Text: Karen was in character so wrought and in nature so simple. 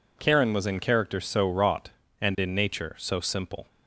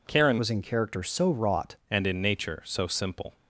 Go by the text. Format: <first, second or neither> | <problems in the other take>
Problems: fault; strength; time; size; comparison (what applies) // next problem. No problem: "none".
first | changes voice from "was" to "wrought"; from 0.3 to 1.7 s; 1.4 s long